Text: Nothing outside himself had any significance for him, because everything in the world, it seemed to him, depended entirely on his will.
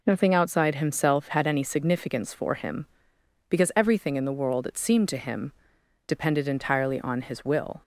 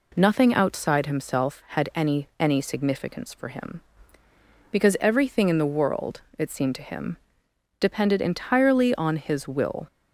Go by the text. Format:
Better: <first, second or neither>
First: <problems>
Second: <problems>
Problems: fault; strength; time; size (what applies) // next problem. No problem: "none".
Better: first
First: none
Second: says "any" twice; at 2.3 s